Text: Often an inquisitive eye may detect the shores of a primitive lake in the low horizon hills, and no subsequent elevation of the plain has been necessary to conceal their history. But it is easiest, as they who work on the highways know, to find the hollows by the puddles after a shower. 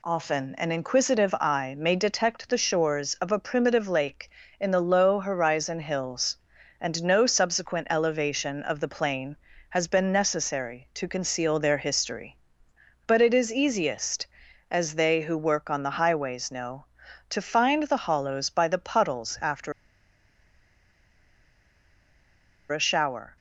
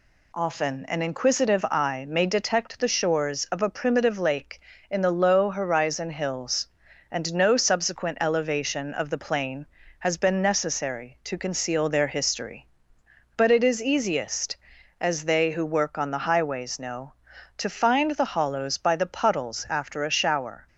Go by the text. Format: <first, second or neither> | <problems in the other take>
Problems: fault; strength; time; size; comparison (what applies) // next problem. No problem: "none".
second | pauses between "after" and "a"; strong; at 19.7 s; 2.9 s long